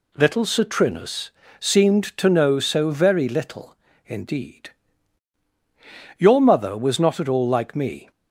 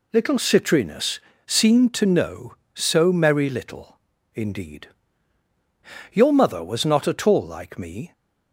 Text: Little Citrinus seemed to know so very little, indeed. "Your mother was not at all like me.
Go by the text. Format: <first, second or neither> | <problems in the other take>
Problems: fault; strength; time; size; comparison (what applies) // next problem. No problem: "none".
first | pauses between "Citrinus" and "seemed"; slight; at 1.1 s; 0.28 s long; slight in the first // says "merry" for "very"; at 3.1 s